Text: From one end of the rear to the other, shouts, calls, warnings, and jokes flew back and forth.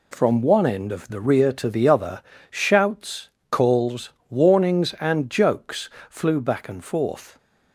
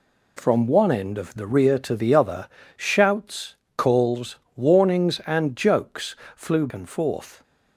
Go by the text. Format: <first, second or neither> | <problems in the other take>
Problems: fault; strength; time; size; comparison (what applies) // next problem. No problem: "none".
first | pauses between "jokes" and "flew"; slight; at 6.1 s; 0.20 s long; slight in the first // skips "back"; at 6.6 s